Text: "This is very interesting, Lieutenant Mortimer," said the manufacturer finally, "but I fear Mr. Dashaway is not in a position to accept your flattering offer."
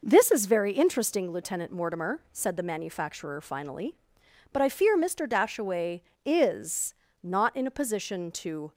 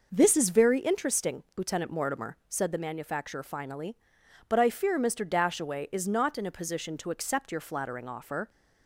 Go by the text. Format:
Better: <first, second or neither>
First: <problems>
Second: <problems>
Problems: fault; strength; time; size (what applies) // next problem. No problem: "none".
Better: second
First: pauses between "is" and "not"; slight; at 6.9 s; 0.28 s long // stops before "accept your flattering offer"; at 8.7 s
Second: none